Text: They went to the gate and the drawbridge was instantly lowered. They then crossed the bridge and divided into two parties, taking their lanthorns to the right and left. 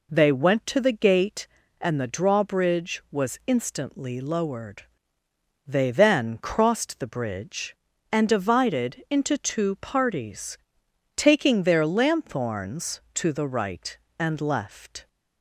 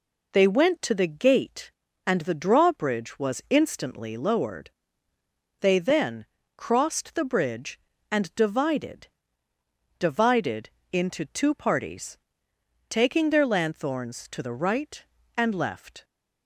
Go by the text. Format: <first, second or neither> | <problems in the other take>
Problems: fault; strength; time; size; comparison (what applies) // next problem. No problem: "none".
first | pauses between "then" and "crossed"; slight; at 6.2 s; 0.30 s long // says "divided" twice; at 9.9 s